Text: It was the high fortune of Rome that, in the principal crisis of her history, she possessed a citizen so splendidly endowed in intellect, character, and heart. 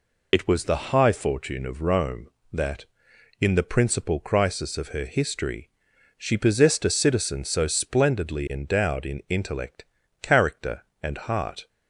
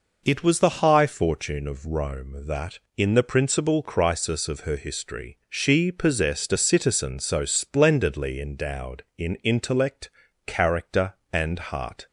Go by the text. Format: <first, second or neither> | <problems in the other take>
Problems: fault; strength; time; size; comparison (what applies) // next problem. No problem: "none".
second | loses the start of "It"; at 0.3 s; 50 ms